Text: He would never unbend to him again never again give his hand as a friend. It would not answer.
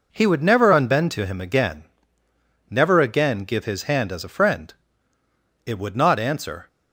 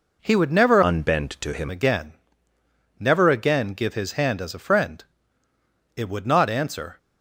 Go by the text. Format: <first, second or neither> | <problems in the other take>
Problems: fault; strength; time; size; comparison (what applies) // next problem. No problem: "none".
first | changes voice from "unbend" to "him"; from 0.8 to 1.6 s; 0.8 s long // pauses between "again" and "never"; noticeable; at 2.1 s; 0.86 s long; noticeable in the first